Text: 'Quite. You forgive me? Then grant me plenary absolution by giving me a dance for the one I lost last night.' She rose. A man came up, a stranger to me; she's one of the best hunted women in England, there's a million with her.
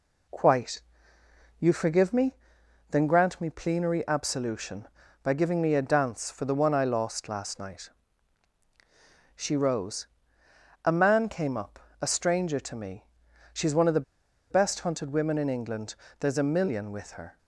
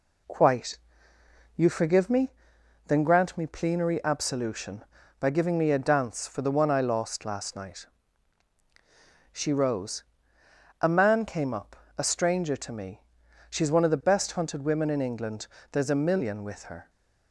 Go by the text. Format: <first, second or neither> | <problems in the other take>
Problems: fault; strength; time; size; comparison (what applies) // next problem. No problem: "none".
second | pauses between "the" and "best"; noticeable; at 14.0 s; 0.48 s long